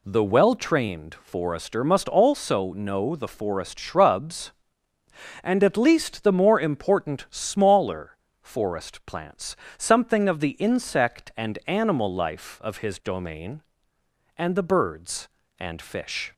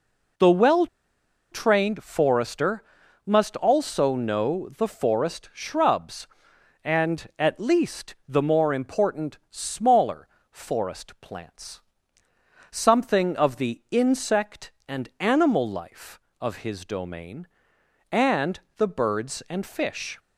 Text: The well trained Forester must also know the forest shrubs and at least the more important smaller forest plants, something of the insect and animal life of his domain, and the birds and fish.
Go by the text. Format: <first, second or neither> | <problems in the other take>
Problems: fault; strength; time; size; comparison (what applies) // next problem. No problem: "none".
first | pauses between "well" and "trained"; noticeable; at 0.8 s; 0.66 s long // pauses between "Forester" and "must"; at 2.8 s; 0.42 s long // pauses between "smaller" and "forest"; slight; at 10.2 s; 0.24 s long; slight in the first // pauses between "and" and "the"; slight; at 18.5 s; 0.18 s long